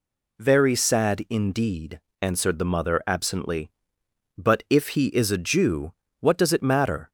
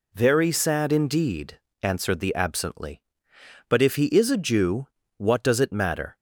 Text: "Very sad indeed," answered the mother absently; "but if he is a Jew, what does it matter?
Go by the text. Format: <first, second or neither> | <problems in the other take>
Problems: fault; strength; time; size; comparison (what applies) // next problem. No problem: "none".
first | skips "mother"; at 2.3 s